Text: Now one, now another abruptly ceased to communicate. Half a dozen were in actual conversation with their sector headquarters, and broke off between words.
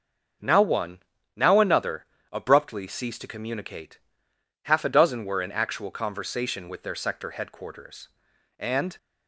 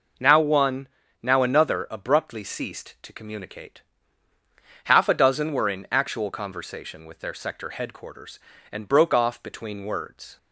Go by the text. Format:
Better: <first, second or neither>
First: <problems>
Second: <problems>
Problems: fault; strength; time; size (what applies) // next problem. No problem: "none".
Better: second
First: starts louder than the rest; until 1.7 s; 6.5 dB // pauses between "another" and "abruptly"; slight; at 2.0 s; 0.26 s long // stops before "broke off between words"; at 8.9 s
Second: none